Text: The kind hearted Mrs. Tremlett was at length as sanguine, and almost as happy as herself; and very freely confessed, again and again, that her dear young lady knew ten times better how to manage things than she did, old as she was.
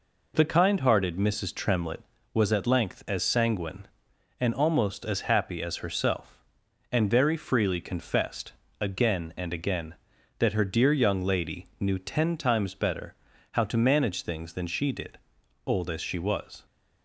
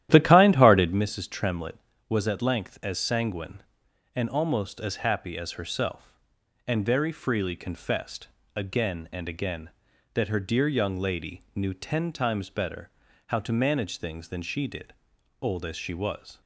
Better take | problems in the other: first | starts louder than the rest; strong; until 1.0 s; 12.5 dB // pauses between "better" and "how"; at 12.9 s; 0.38 s long; also in the first

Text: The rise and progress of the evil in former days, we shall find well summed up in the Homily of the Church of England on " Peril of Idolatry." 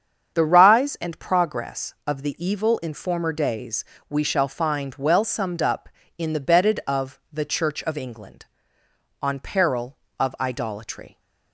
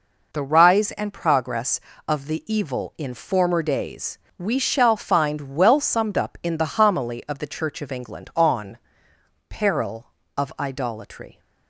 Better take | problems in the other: second | starts louder than the rest; strong; until 1.4 s; 7.5 dB // says "Bedded" for "Homily"; at 6.3 s

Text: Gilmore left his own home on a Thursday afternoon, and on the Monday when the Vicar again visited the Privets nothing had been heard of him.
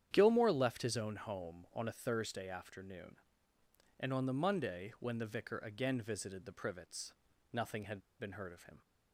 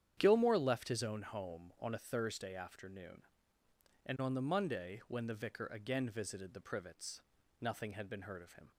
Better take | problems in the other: second | starts louder than the rest; strong; until 1.1 s; 9.5 dB; strong in the second // pauses between "Privets" and "nothing"; at 7.1 s; 0.40 s long; also in the second // pauses between "had" and "been"; slight; at 8.0 s; 0.19 s long

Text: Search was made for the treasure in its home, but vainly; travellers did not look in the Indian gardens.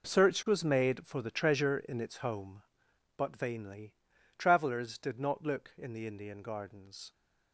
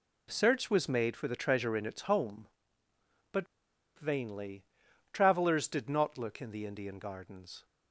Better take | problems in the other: first | pauses between "but" and "vainly"; noticeable; at 3.4 s; 0.50 s long

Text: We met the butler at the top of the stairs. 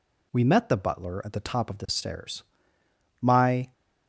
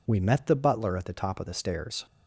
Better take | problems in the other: second | goes on to say "My"; from 3.1 s on; 0.52 s long

